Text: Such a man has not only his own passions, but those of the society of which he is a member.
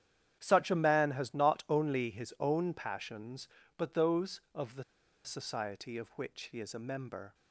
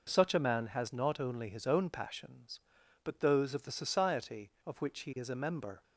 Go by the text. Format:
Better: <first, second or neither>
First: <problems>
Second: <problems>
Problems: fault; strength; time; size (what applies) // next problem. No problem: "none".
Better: second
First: starts louder than the rest; strong; until 1.4 s; 9.5 dB // pauses between "the" and "society"; at 4.8 s; 0.42 s long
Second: none